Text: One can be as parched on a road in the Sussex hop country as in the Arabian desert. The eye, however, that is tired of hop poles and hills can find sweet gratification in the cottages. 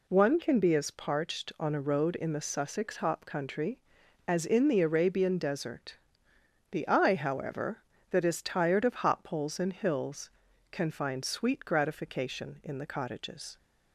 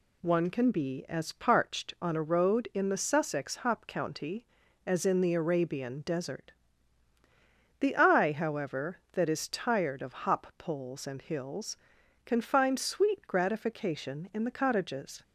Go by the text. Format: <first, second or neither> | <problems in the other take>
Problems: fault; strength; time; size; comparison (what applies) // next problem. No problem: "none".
first | says "county" for "country"; at 3.8 s